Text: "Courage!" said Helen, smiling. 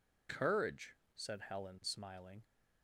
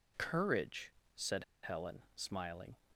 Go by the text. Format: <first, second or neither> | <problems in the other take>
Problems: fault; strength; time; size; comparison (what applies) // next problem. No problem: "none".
first | pauses between "said" and "Helen"; slight; at 1.4 s; 0.19 s long